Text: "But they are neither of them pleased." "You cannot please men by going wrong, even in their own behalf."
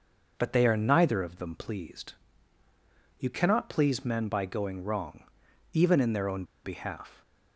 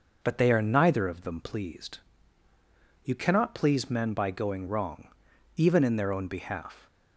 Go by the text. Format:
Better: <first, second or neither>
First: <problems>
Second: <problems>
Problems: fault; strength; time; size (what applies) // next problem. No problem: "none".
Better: second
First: pauses between "own" and "behalf"; slight; at 6.4 s; 0.21 s long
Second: none